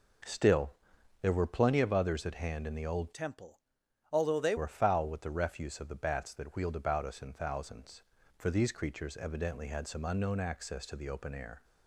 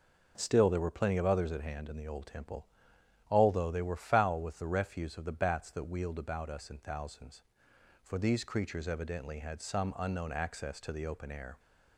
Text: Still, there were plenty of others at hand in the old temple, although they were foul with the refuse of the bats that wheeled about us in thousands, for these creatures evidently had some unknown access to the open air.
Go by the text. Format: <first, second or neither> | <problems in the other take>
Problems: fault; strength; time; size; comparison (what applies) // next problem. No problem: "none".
second | changes voice from "temple" to "they"; from 3.1 to 4.5 s; 1.4 s long